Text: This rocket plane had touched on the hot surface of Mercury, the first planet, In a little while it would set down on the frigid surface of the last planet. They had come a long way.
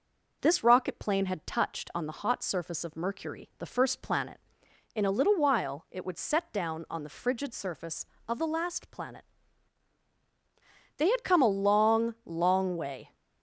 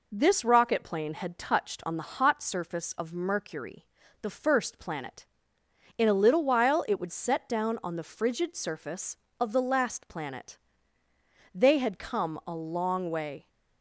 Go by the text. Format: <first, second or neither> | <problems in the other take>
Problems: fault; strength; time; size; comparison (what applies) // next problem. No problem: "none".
second | says "long" twice; at 12.2 s